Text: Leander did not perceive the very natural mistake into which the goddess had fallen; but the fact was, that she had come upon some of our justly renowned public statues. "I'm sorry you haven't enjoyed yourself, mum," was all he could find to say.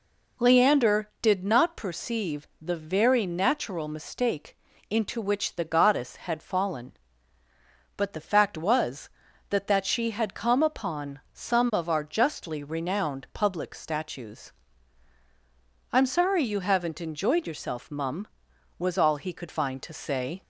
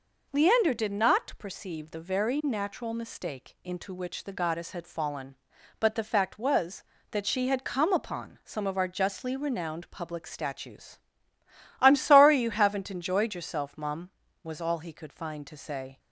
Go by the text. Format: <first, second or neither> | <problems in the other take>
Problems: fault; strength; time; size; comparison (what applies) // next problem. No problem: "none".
second | pauses between "perceive" and "the"; slight; at 2.4 s; 0.16 s long // pauses between "mistake" and "into"; slight; at 4.5 s; 0.32 s long // says "that" twice; at 9.6 s